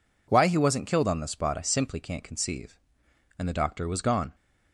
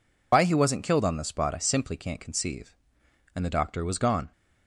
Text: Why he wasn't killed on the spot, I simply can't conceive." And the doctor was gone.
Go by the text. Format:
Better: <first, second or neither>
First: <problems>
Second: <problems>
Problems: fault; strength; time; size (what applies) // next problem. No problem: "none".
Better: first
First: none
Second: loses the start of "Why"; at 0.3 s; 80 ms